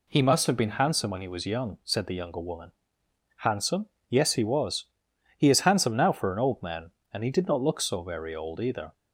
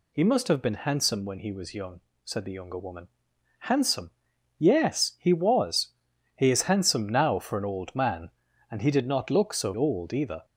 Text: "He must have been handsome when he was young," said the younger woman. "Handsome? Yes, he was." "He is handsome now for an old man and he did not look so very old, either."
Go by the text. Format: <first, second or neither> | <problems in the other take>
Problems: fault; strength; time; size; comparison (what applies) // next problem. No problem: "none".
first | skips "very"; at 9.7 s